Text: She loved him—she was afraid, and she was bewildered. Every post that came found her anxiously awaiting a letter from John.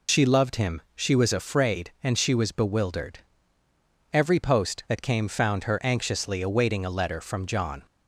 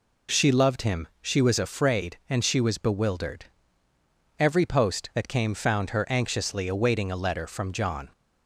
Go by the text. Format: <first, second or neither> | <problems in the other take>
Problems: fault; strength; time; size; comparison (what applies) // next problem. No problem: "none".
second | loses the start of "She"; at 0.0 s; 60 ms